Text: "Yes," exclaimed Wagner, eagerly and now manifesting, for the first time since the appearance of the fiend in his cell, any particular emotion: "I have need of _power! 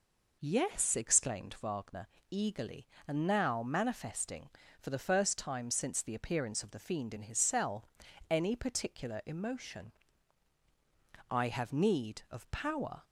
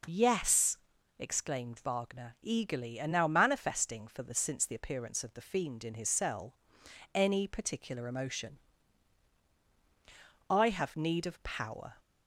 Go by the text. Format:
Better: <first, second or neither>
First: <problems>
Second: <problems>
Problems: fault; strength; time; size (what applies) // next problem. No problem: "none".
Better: first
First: none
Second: skips "first time"; at 4.3 s